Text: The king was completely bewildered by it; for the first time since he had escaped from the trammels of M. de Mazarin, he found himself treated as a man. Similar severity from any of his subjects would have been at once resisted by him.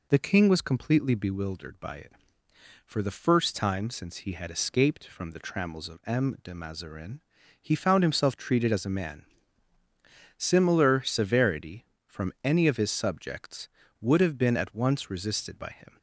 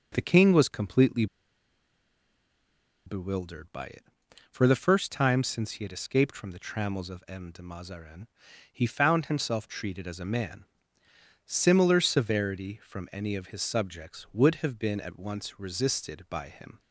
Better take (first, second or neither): first